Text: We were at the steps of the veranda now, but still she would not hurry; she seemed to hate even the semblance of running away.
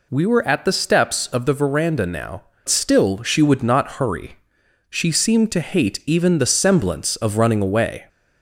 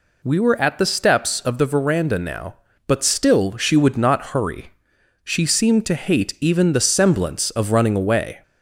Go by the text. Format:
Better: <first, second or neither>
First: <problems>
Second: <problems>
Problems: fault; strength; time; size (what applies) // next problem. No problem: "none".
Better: second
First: skips "but"; at 2.5 s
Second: none